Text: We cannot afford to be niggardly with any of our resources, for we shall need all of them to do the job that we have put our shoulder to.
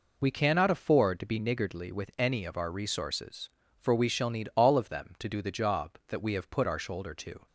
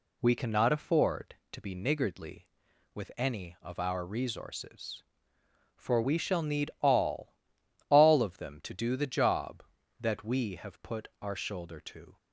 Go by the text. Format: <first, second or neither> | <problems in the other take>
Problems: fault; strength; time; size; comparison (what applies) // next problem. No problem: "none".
first | says "all" twice; at 7.8 s